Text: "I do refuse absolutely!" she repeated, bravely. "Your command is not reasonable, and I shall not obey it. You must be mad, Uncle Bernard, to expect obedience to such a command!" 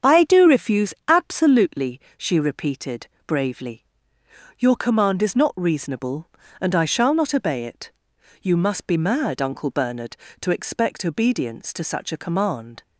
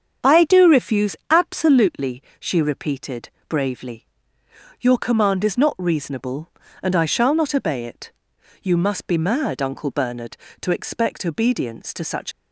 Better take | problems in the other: first | starts louder than the rest; strong; until 1.3 s; 7.5 dB; strong in the first // stops before "a command"; at 12.3 s

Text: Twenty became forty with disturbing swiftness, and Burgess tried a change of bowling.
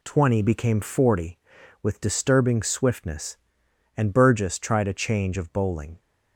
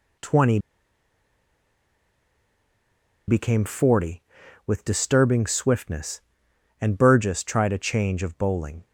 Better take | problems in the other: first | pauses between "Twenty" and "became"; strong; at 0.5 s; 2.6 s long

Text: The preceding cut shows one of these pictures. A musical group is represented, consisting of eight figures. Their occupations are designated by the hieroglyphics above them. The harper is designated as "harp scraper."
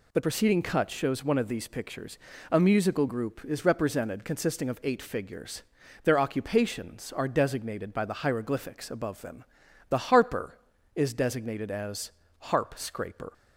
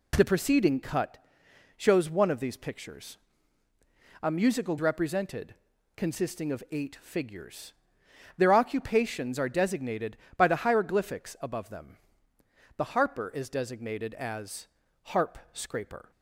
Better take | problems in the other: first | pauses between "cut" and "shows"; noticeable; at 1.1 s; 0.58 s long // skips "group is"; at 4.7 s // pauses between "as" and "harp"; slight; at 14.6 s; 0.34 s long; slight in the first

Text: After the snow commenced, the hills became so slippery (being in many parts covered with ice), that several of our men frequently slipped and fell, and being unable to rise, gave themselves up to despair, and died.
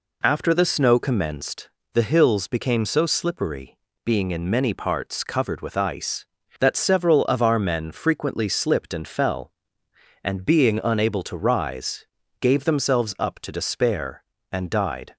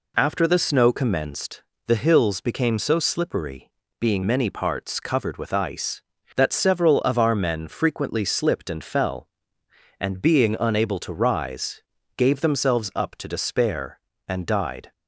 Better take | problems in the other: first | skips "in"; at 4.2 s

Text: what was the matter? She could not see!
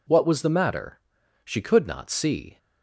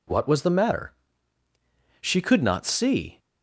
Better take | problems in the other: neither | none

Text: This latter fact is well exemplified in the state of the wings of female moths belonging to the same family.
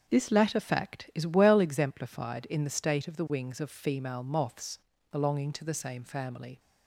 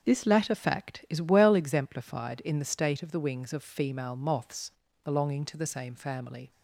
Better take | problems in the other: neither | starts louder than the rest; the same in both // pauses between "moths" and "belonging"; slight; the same in both

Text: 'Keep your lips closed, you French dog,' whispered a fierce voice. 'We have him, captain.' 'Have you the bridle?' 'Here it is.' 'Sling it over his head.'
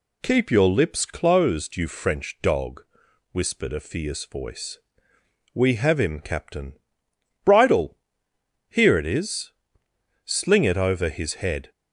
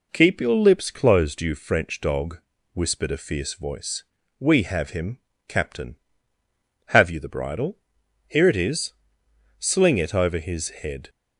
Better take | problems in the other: second | skips "Have you the"; at 7.0 s

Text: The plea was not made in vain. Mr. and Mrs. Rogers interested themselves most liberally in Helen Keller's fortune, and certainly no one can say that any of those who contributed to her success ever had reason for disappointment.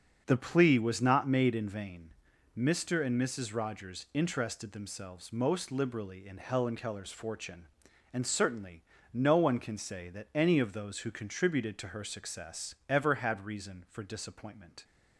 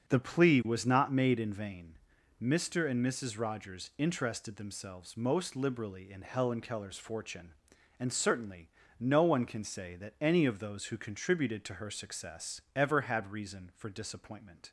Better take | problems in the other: neither | starts louder than the rest; the same in both // pauses between "certainly" and "no"; slight; the same in both // pauses between "success" and "ever"; slight; the same in both

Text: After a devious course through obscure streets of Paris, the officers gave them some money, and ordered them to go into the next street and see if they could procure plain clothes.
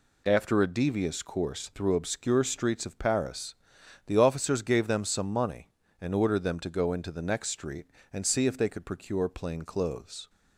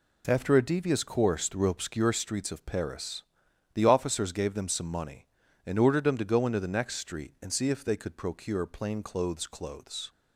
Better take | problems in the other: first | says "clothes" twice; at 9.4 s

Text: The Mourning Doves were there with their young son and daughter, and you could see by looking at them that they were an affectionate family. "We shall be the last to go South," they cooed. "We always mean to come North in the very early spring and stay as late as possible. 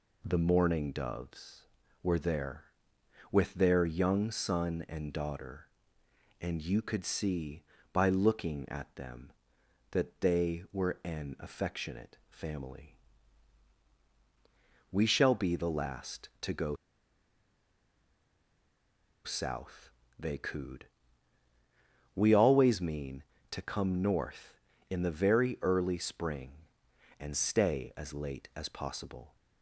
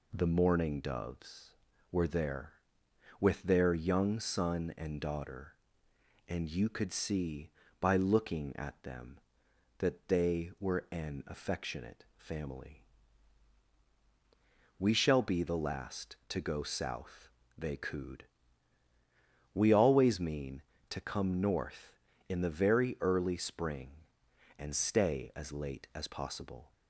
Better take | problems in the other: second | pauses between "go" and "South"; strong; at 16.7 s; 2.4 s long

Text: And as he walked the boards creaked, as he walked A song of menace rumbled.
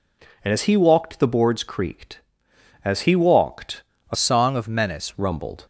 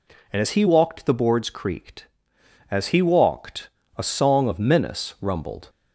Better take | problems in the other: second | pauses between "walked" and "A"; slight; at 3.8 s; 0.26 s long; slight in the second // changes voice from "song" to "menace"; from 4.1 to 5.1 s; 1.0 s long

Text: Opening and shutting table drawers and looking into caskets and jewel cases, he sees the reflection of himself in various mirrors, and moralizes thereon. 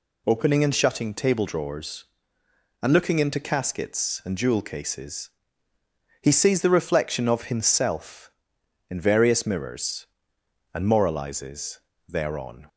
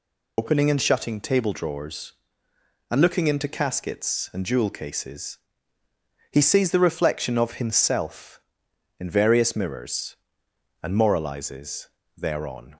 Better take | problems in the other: first | loses the start of "Opening"; at 0.3 s; 55 ms // pauses between "moralizes" and "thereon"; slight; at 11.8 s; 0.30 s long; slight in the first

